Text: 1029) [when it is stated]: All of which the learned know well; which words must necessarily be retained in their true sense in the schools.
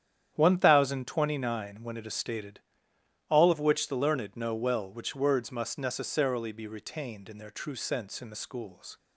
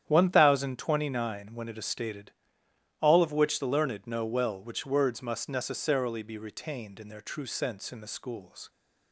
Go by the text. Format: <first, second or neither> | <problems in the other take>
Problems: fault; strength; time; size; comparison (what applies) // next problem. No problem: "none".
neither | starts louder than the rest; strong; the same in both